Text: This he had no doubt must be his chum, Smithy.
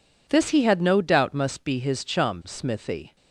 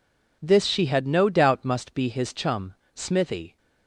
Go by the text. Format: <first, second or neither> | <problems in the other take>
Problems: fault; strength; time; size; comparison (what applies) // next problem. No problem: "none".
first | says "she" for "he"; at 0.6 s